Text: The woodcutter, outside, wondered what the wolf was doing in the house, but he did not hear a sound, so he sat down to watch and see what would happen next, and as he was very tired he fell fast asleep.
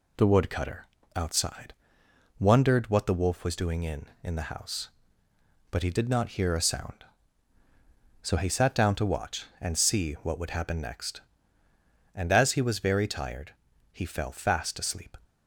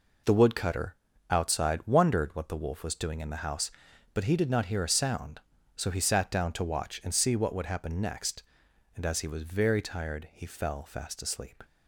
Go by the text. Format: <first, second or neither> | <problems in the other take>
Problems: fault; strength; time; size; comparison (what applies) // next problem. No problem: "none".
second | says "in" twice; at 4.2 s // pauses between "tired" and "he"; at 13.5 s; 0.38 s long